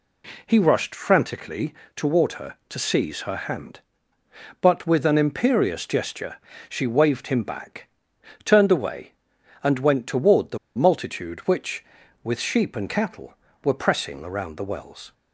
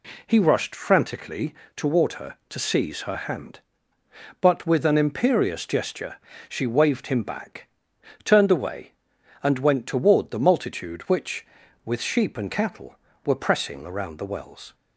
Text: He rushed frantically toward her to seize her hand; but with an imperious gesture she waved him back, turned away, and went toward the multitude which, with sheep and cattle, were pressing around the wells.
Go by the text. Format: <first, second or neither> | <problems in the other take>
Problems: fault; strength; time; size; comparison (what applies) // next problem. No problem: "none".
second | pauses between "frantically" and "toward"; slight; at 1.7 s; 0.22 s long; slight in the second // pauses between "gesture" and "she"; slight; at 6.3 s; 0.30 s long; slight in the second // pauses between "the" and "multitude"; slight; at 10.5 s; 0.19 s long